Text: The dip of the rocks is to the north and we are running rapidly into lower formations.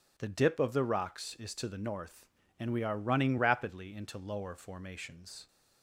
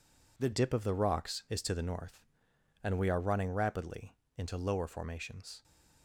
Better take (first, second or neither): first